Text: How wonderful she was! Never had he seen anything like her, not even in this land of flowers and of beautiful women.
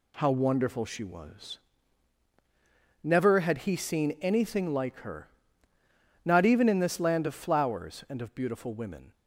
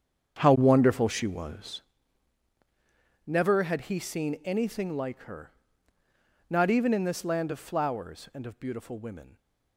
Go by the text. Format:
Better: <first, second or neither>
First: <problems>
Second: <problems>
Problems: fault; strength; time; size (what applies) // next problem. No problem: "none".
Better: first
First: none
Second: starts louder than the rest; strong; until 1.9 s; 8 dB